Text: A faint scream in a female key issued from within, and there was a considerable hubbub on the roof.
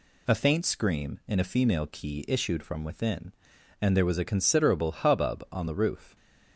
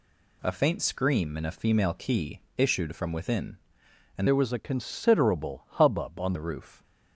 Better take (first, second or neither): first